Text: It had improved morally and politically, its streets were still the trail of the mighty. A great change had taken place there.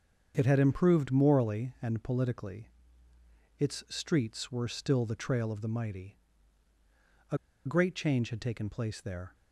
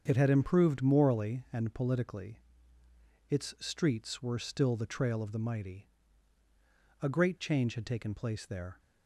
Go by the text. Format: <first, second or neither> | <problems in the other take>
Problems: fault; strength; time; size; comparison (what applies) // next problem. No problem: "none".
second | starts louder than the rest; strong; until 1.3 s; 7 dB; strong in the second // pauses between "A" and "great"; slight; at 7.3 s; 0.28 s long